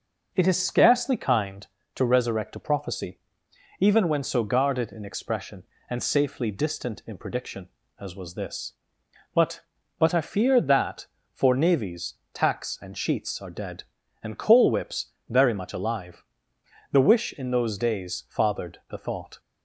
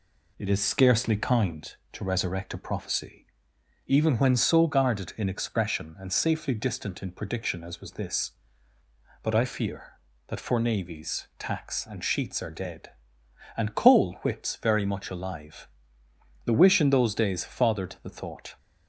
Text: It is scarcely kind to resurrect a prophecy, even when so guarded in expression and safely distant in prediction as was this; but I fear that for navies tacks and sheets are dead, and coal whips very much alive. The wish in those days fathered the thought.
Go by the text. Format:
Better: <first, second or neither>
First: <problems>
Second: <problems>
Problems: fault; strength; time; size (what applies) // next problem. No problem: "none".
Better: second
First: says "but" twice; at 9.9 s // pauses between "navies" and "tacks"; slight; at 12.1 s; 0.18 s long // pauses between "whips" and "very"; slight; at 15.1 s; 0.16 s long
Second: none